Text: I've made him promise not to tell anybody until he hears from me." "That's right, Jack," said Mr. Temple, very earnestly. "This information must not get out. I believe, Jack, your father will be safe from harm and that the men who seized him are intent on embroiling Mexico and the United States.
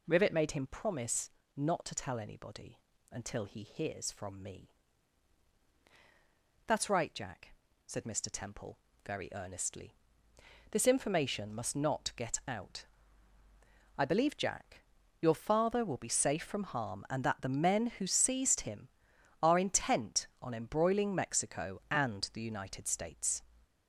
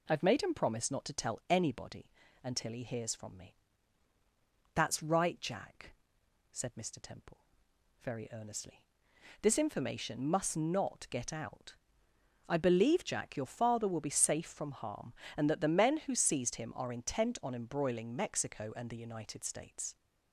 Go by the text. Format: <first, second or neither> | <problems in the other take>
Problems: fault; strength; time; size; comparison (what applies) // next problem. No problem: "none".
second | says "Rivet" for "I've"; at 0.0 s // pauses between "promise" and "not"; slight; at 1.3 s; 0.24 s long // pauses between "anybody" and "until"; slight; at 2.7 s; 0.32 s long; slight in the second